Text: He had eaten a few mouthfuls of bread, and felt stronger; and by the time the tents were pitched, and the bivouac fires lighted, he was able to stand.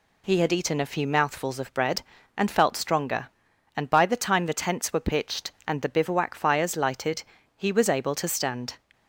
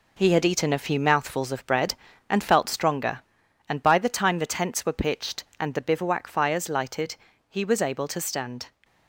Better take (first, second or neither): first